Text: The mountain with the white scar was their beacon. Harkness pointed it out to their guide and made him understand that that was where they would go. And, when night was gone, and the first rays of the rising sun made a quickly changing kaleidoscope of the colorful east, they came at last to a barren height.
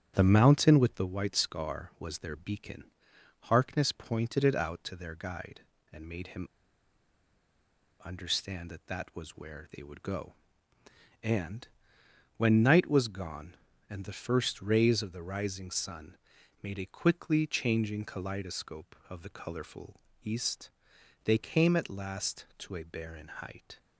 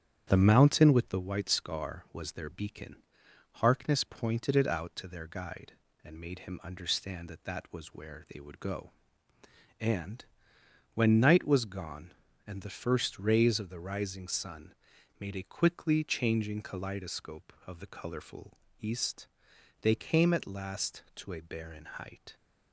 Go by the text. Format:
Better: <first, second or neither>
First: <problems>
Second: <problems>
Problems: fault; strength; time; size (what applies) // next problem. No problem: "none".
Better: second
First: starts louder than the rest; strong; until 1.1 s; 8.5 dB // pauses between "him" and "understand"; strong; at 6.4 s; 1.5 s long // pauses between "sun" and "made"; noticeable; at 16.1 s; 0.46 s long // pauses between "colorful" and "east"; slight; at 19.9 s; 0.24 s long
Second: starts louder than the rest; strong; until 1.2 s; 8.5 dB // pauses between "sun" and "made"; noticeable; at 14.7 s; 0.46 s long // pauses between "colorful" and "east"; slight; at 18.5 s; 0.24 s long